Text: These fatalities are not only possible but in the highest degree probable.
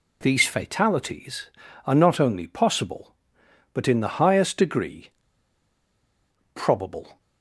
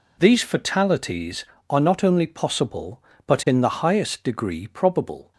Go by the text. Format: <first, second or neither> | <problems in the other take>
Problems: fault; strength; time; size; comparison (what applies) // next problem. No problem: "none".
second | pauses between "degree" and "probable"; strong; at 5.0 s; 1.4 s long